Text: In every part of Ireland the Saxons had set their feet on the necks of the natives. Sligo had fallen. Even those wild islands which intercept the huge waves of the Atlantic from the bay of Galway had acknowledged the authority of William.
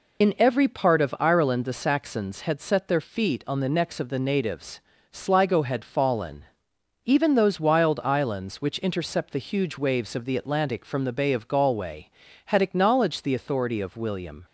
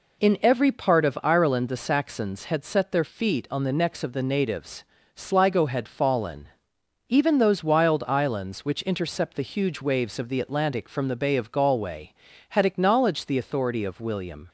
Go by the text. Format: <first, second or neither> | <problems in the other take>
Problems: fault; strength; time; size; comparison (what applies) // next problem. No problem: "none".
second | loses the start of "In"; at 0.2 s; 35 ms